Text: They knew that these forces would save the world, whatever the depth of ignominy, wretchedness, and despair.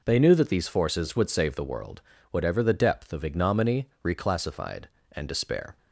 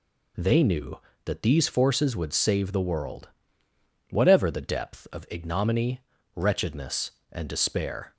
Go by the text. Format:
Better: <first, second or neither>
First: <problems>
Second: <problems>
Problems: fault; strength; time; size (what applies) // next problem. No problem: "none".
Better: second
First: says "reclassified" for "wretchedness"; at 4.0 s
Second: none